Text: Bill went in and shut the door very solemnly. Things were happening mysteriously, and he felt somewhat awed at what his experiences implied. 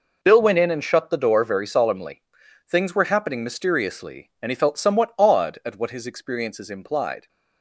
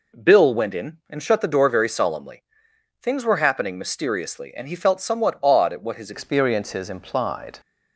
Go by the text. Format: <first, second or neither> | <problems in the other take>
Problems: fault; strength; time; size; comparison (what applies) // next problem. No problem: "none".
first | changes voice at "experiences"; from 6.1 s on; 1.4 s long